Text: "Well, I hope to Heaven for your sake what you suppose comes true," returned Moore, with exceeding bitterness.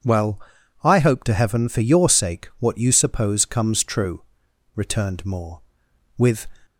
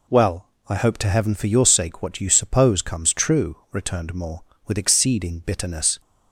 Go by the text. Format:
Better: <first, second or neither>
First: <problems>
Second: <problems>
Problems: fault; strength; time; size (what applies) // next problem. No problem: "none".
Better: second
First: stops before "exceeding bitterness"; at 6.6 s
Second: none